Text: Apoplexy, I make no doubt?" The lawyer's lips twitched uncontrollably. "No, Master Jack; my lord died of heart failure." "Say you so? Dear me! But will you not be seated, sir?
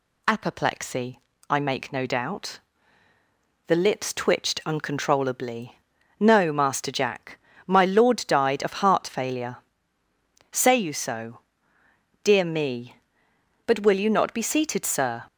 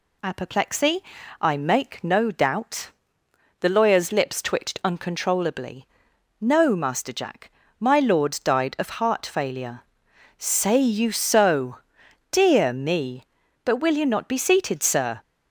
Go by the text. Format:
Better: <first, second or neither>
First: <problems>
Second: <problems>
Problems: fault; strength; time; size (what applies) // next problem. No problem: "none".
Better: second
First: skips "lawyer's"; at 3.7 s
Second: none